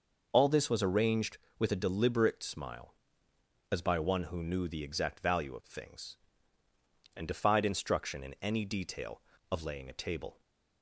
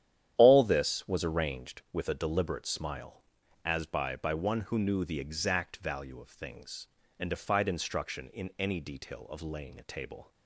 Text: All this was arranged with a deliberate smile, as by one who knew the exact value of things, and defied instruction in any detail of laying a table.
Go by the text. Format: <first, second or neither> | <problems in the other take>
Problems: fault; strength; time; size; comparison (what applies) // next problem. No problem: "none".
first | starts louder than the rest; strong; until 1.3 s; 10.5 dB // says "by" twice; at 4.1 s